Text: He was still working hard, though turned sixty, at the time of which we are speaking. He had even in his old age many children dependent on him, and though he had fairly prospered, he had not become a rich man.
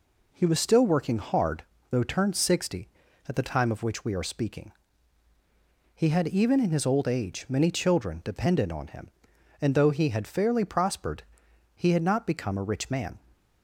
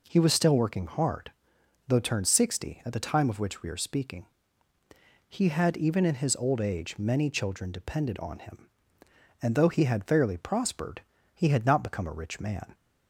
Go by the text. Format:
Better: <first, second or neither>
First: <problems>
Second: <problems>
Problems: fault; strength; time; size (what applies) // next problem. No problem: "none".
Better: neither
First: none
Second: none